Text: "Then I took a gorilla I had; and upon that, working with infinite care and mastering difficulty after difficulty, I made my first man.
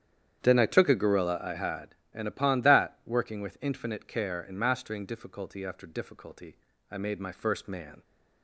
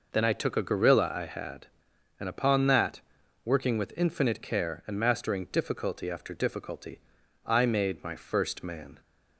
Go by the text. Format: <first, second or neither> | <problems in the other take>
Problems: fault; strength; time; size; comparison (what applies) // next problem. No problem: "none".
second | starts louder than the rest; strong; until 1.5 s; 9 dB